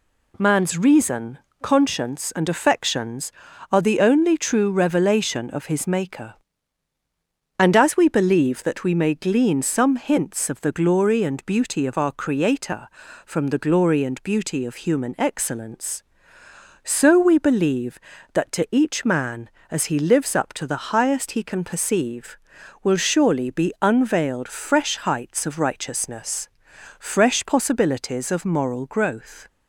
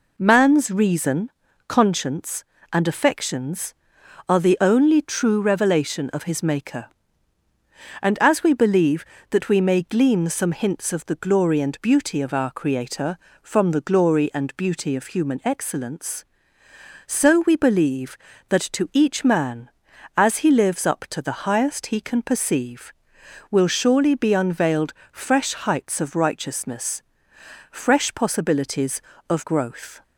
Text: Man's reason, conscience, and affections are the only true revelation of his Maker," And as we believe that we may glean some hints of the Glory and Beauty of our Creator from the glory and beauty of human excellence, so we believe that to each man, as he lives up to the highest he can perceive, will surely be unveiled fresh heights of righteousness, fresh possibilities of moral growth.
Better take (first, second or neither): first